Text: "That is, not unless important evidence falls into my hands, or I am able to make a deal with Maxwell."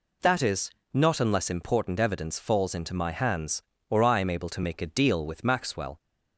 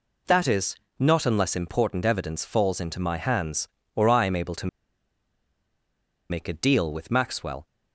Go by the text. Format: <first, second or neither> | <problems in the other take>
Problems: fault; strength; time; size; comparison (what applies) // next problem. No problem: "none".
first | pauses between "to" and "make"; strong; at 4.6 s; 1.6 s long